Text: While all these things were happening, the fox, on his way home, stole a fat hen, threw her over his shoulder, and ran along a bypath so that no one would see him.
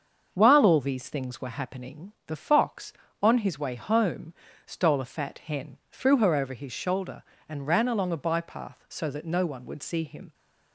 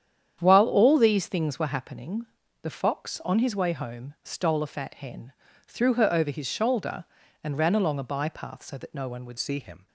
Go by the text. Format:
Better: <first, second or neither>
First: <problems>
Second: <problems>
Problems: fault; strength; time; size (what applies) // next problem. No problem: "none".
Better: first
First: starts louder than the rest; until 1.3 s; 6.5 dB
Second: starts louder than the rest; strong; until 1.4 s; 9 dB // changes voice at "see"; from 9.3 s on; 0.5 s long